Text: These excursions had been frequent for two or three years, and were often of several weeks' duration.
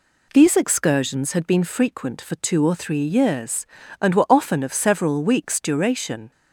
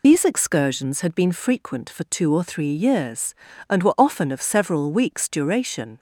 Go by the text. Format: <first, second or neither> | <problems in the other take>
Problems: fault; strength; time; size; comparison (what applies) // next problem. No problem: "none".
first | loses the start of "These"; at 0.0 s; 60 ms